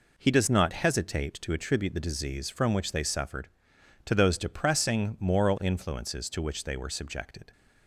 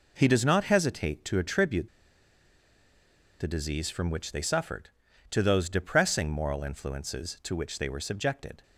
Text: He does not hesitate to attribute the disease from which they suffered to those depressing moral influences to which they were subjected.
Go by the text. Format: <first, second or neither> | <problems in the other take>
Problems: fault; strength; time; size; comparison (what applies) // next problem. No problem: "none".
first | pauses between "attribute" and "the"; strong; at 1.8 s; 1.5 s long